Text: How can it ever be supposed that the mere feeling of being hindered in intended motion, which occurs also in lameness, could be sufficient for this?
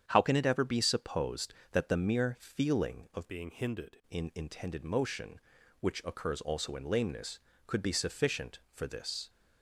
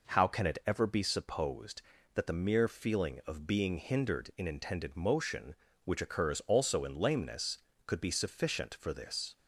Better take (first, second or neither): second